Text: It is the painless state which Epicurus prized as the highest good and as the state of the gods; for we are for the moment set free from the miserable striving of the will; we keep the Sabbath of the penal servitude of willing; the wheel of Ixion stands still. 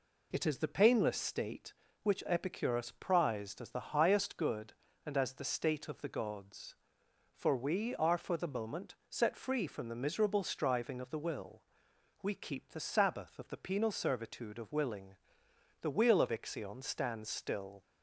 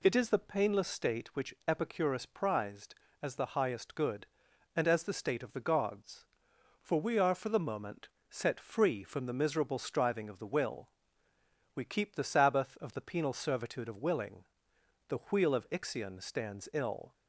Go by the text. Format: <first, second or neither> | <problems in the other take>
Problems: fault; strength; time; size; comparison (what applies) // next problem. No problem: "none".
first | pauses between "moment" and "set"; slight; at 8.0 s; 0.20 s long; slight in the first // says "ill" for "still"; at 16.7 s